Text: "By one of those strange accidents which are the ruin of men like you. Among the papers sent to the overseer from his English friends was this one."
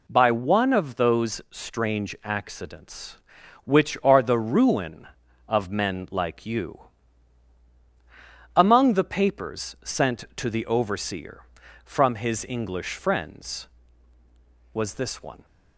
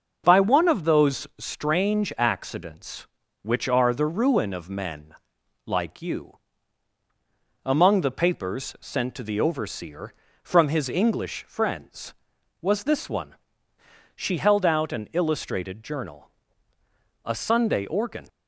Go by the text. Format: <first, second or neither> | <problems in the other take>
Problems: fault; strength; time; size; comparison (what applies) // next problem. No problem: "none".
first | starts louder than the rest; until 1.2 s; 6.5 dB // pauses between "men" and "like"; noticeable; at 5.1 s; 0.54 s long // goes on to say "She held out an illustrated journal a Sunday organ"; strong; from 14.1 s on; 4.1 s long